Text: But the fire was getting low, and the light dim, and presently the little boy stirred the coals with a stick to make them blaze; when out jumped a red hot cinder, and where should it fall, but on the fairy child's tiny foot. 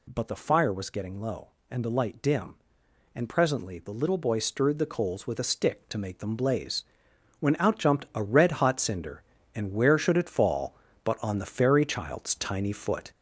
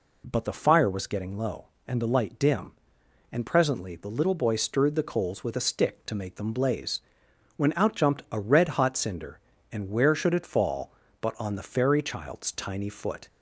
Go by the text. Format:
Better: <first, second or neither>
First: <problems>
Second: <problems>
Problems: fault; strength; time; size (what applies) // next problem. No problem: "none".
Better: second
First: gets louder; noticeable; throughout; 4.5 dB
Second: none